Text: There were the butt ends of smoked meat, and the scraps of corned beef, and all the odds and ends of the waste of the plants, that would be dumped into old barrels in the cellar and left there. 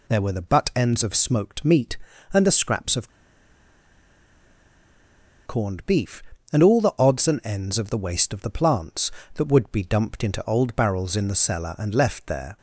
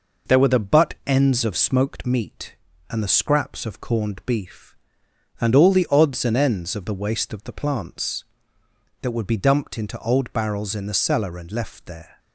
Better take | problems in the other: second | pauses between "of" and "corned"; strong; at 3.1 s; 2.3 s long

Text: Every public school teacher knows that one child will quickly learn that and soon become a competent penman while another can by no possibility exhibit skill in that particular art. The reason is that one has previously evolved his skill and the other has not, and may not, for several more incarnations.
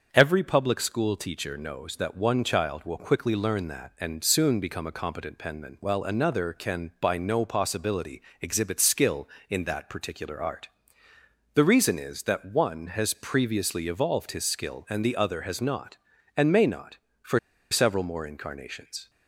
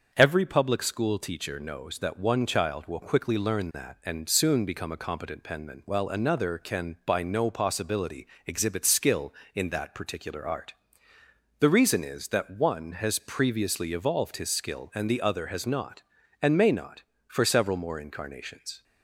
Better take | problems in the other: second | starts louder than the rest; until 1.1 s; 7 dB; also in the second // pauses between "possibility" and "exhibit"; slight; at 8.1 s; 0.20 s long; slight in the second // pauses between "for" and "several"; slight; at 17.3 s; 0.33 s long

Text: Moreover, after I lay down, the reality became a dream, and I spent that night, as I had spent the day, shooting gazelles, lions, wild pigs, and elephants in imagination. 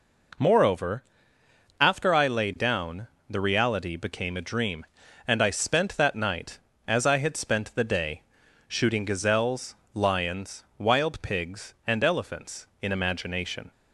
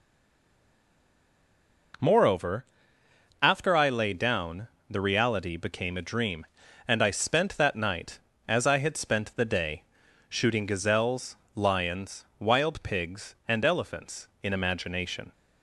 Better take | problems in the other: first | stays silent before the first word; noticeable; until 1.9 s; 1.9 s long

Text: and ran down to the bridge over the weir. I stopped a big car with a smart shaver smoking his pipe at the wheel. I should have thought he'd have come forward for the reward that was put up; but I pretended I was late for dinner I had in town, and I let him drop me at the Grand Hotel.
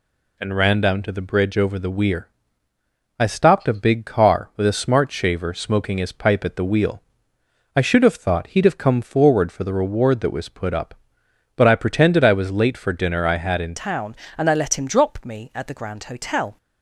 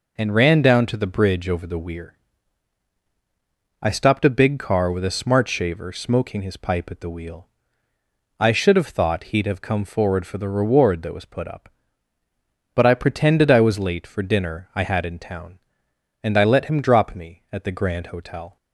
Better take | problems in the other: second | changes voice at "town"; from 13.7 s on; 2.8 s long

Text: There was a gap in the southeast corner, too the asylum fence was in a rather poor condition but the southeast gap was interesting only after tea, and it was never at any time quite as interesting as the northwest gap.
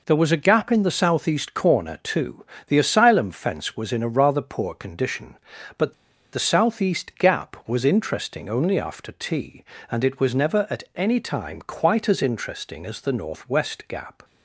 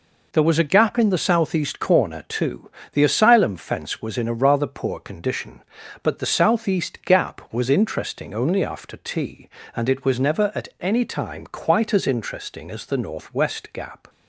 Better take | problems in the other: second | pauses between "too" and "the"; slight; at 2.4 s; 0.24 s long; slight in the second // pauses between "but" and "the"; at 5.9 s; 0.38 s long

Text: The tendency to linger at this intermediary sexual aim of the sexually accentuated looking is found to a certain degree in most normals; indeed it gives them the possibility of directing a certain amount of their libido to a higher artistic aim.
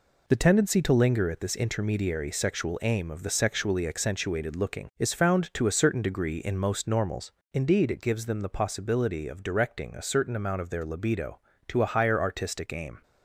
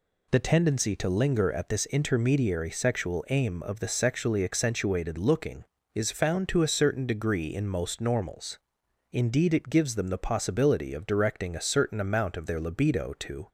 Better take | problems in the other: first | stops before "a higher artistic aim"; at 13.4 s

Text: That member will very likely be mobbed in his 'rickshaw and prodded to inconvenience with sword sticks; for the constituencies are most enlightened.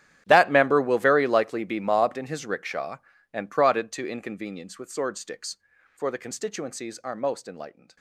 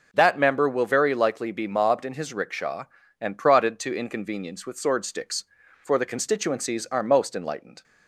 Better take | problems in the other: second | gets quieter; strong; throughout; 19.5 dB

